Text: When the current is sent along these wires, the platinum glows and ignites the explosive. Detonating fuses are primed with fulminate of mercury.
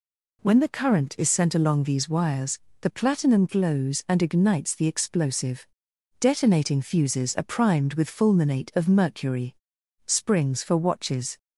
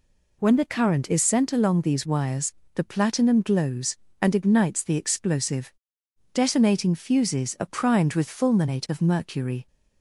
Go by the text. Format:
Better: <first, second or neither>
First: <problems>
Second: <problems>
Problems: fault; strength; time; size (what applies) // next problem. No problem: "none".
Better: second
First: goes on to say "Springs for watches"; from 10.0 s on; 1.3 s long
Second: none